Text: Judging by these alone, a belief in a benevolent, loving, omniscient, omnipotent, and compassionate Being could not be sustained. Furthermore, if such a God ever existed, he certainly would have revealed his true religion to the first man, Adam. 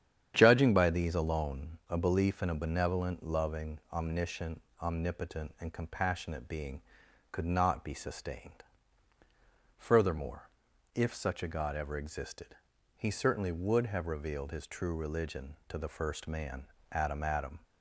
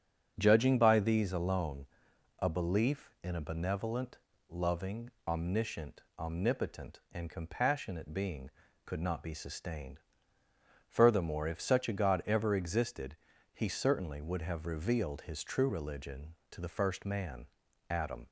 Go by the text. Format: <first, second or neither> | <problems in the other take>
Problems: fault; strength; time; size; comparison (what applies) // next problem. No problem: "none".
second | starts louder than the rest; strong; until 1.3 s; 9 dB; strong in the second // says "Adam" twice; at 17.2 s